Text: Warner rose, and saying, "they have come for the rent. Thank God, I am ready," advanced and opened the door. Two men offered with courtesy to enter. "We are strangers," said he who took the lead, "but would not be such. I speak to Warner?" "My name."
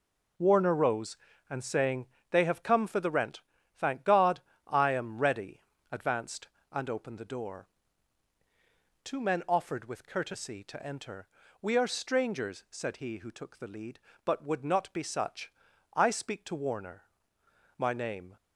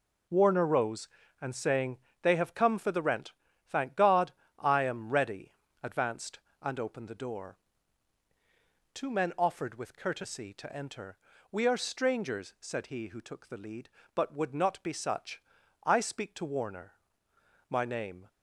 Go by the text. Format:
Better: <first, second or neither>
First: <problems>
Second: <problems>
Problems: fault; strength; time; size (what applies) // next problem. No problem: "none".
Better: neither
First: none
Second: none